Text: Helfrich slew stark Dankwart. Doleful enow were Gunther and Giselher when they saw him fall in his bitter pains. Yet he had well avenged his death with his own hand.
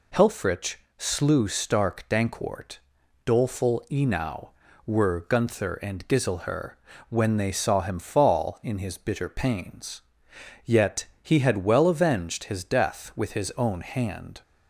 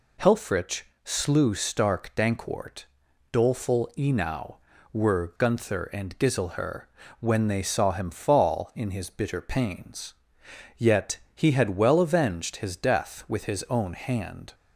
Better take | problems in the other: neither | pauses between "Helfrich" and "slew"; slight; the same in both // pauses between "Giselher" and "when"; slight; the same in both // pauses between "Yet" and "he"; slight; the same in both

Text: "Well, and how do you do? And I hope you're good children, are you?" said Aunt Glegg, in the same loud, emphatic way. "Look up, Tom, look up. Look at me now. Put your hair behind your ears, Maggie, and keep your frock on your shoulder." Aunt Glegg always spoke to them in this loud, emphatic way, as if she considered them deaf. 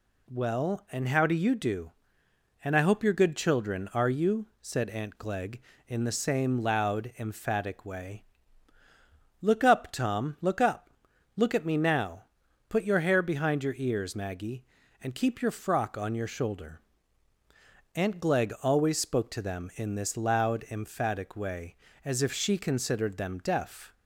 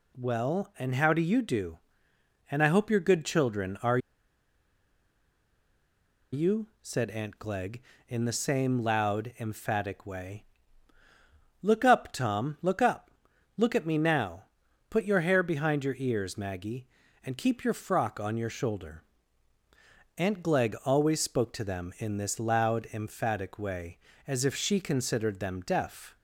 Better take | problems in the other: first | pauses between "are" and "you"; strong; at 3.9 s; 2.3 s long

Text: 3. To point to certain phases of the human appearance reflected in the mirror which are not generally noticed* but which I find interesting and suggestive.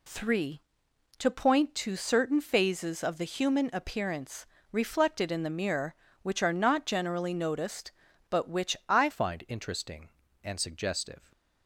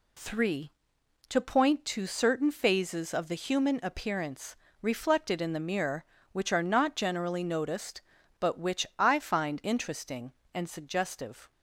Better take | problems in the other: second | pauses between "appearance" and "reflected"; slight; at 4.4 s; 0.26 s long; slight in the second // changes voice at "find"; from 9.0 s on; 2.3 s long

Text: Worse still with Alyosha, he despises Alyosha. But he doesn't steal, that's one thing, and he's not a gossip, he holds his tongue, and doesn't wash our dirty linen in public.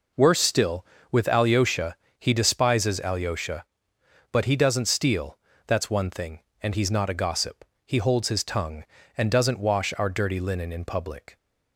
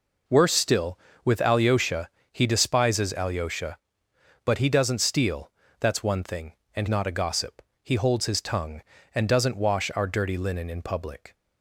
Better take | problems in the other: first | skips "he's"; at 6.8 s

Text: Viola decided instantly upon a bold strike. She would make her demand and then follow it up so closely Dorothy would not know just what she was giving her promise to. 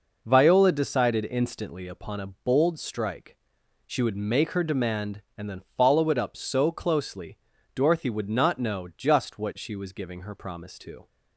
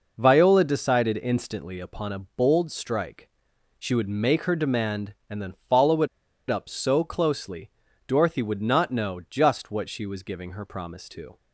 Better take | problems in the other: first | pauses between "it" and "up"; at 6.0 s; 0.42 s long // pauses between "closely" and "Dorothy"; at 7.7 s; 0.38 s long; also in the first

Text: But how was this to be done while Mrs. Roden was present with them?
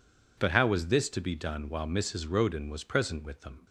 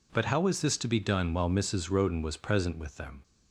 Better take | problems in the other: neither | none

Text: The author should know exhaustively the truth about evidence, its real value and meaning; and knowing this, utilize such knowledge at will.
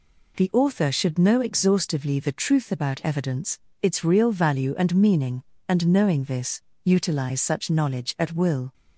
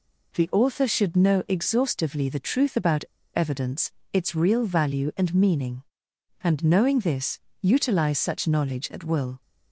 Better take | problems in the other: first | pauses between "about" and "evidence"; slight; at 3.0 s; 0.30 s long

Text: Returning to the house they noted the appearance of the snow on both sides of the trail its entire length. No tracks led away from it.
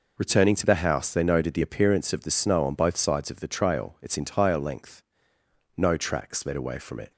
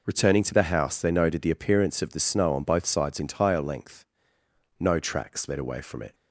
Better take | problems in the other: first | skips "of the trail its"; at 3.1 s

